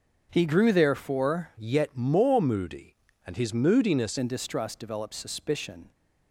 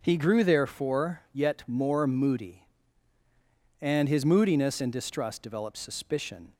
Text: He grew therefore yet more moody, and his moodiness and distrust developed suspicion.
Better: second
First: starts louder than the rest; until 1.3 s; 6.5 dB // changes voice from "yet" to "moodiness"; from 1.5 to 4.1 s; 2.6 s long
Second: none

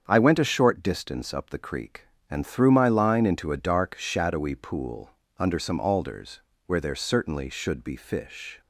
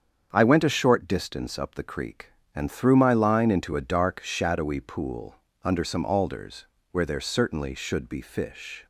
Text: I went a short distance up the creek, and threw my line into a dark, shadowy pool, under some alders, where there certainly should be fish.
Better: neither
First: starts louder than the rest; strong; until 1.0 s; 7.5 dB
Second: starts louder than the rest; strong; until 1.3 s; 7.5 dB

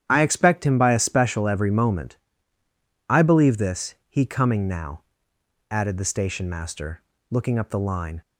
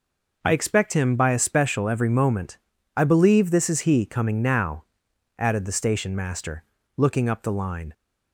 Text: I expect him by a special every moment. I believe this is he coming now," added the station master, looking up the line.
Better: second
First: starts louder than the rest; strong; until 1.0 s; 10 dB // skips "is"; at 4.0 s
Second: none

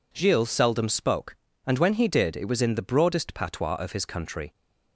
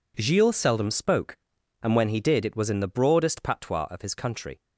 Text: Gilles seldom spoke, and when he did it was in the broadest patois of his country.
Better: neither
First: none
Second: none

